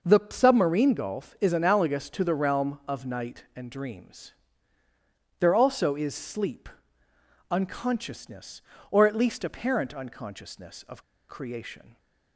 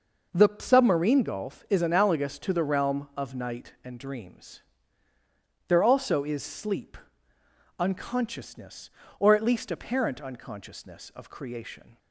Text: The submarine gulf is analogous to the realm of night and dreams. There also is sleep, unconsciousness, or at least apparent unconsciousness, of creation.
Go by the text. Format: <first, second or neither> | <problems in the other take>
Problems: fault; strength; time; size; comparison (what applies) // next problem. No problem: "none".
second | pauses between "of" and "creation"; slight; at 11.0 s; 0.26 s long